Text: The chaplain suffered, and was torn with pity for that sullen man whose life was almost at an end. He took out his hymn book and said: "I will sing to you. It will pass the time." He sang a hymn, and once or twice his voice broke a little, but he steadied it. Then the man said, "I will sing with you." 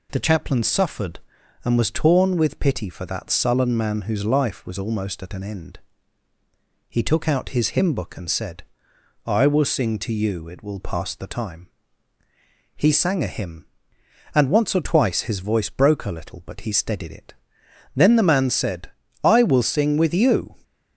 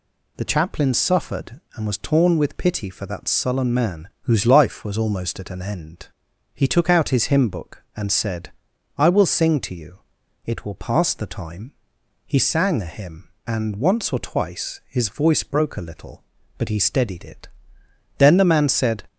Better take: first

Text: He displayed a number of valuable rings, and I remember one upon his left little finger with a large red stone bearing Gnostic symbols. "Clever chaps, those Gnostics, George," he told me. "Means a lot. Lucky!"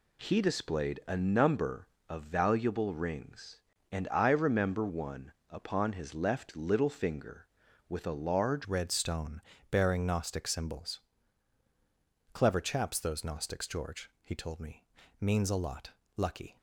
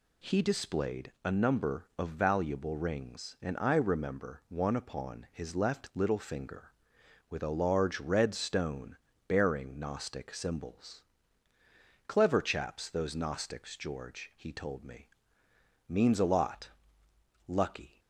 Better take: second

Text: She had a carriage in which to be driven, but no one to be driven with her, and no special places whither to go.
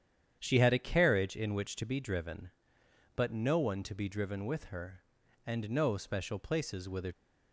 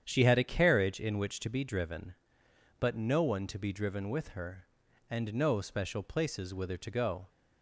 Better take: second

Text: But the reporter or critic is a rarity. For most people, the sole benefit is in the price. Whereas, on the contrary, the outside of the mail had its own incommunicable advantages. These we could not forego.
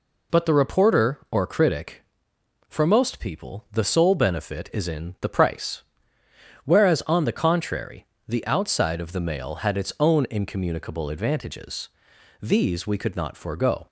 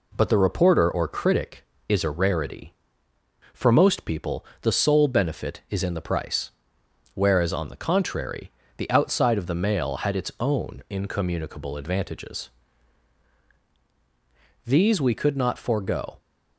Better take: second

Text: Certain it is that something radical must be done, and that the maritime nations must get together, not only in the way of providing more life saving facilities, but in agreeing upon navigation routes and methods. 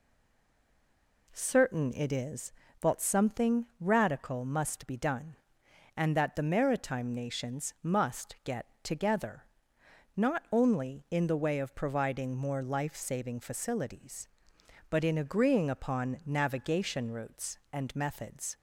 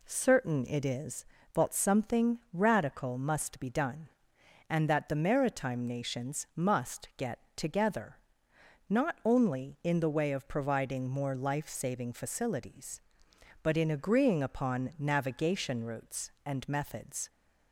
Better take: second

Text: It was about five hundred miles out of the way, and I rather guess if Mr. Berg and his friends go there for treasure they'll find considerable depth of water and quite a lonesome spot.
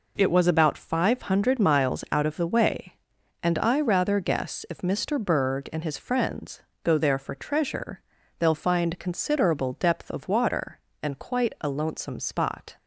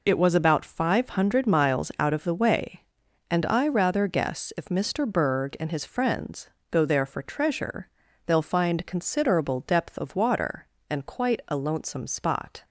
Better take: first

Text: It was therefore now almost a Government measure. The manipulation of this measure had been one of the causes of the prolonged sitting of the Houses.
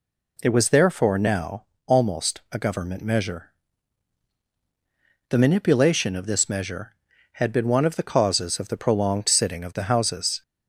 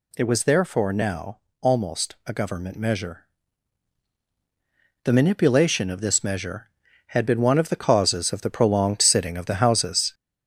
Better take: first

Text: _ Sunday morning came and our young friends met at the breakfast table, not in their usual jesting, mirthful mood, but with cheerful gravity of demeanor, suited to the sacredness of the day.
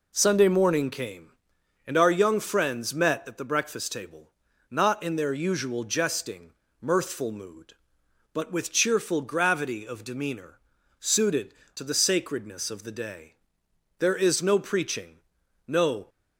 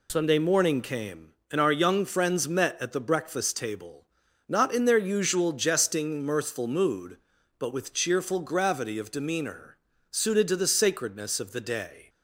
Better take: second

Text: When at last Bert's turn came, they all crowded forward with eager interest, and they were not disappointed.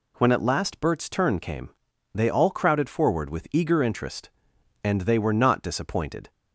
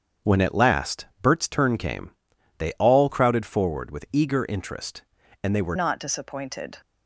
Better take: first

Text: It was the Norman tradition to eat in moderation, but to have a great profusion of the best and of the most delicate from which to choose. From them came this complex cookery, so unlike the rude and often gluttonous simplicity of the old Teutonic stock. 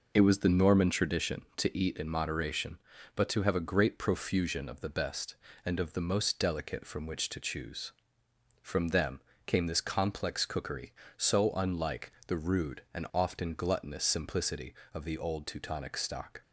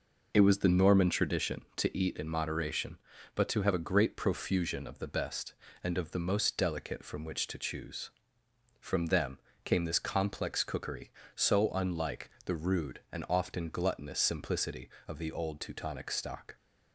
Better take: neither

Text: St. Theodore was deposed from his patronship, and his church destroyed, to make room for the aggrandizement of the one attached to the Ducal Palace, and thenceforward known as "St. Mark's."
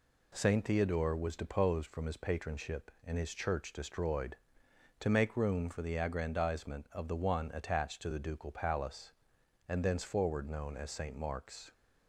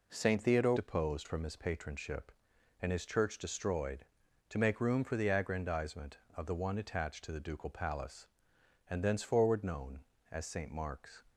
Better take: first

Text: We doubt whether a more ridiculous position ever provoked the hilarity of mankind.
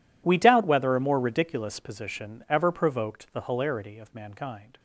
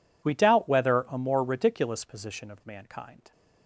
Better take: first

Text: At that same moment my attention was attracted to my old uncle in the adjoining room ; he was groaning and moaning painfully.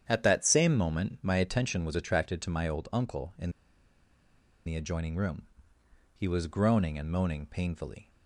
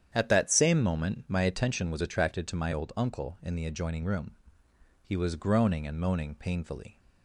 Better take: second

